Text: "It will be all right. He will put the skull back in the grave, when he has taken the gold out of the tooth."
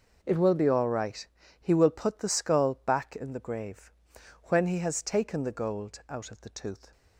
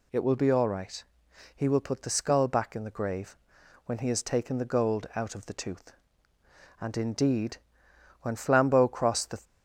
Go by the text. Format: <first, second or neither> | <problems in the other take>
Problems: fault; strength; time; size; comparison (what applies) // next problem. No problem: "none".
first | goes on to say "And indeed when Flambeau crossed the"; strong; from 6.7 s on; 2.6 s long